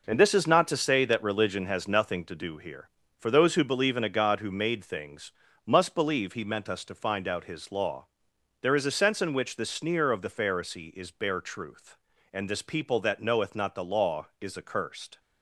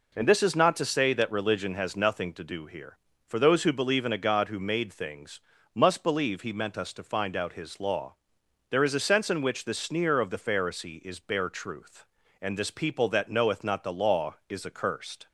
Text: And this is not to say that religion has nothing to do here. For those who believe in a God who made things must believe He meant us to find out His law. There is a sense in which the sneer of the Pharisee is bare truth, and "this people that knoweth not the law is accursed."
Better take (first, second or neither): second